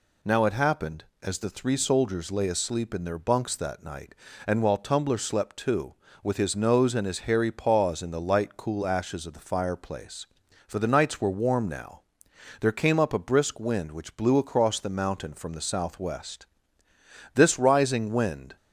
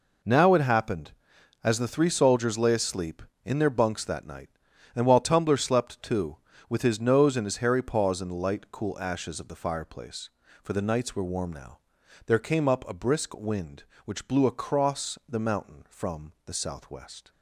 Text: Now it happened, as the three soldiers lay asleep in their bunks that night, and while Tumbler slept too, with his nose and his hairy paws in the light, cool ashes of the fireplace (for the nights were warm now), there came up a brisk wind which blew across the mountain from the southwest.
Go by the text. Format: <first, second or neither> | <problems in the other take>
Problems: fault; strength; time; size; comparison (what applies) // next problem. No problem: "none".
second | goes on to say "This rising wind"; noticeable; from 17.3 s on; 1.2 s long